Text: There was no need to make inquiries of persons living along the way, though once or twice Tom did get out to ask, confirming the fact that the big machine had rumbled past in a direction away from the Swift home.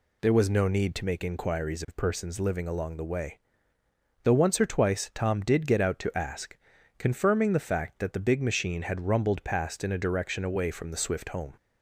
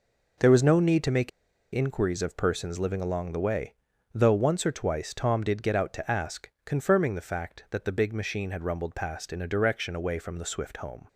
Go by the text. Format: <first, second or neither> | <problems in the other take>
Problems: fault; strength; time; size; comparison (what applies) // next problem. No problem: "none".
first | pauses between "make" and "inquiries"; at 1.2 s; 0.45 s long